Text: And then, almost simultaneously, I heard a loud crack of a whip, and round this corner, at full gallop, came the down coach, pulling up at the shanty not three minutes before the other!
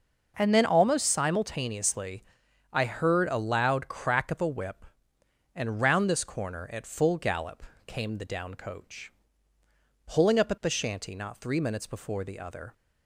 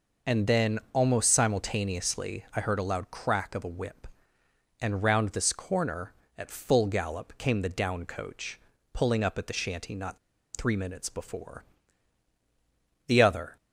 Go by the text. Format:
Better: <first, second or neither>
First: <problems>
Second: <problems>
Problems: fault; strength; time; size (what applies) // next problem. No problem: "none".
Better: first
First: none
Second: pauses between "not" and "three"; at 10.1 s; 0.37 s long // pauses between "before" and "the"; strong; at 11.6 s; 1.4 s long